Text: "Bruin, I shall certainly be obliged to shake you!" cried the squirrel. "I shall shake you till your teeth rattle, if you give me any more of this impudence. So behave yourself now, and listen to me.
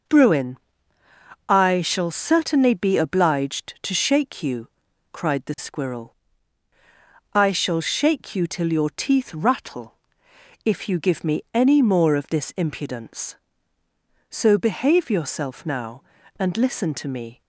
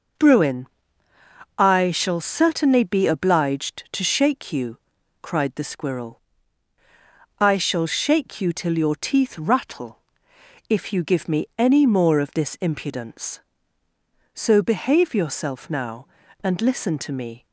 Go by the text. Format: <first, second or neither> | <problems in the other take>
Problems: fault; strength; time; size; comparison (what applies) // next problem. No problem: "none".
neither | none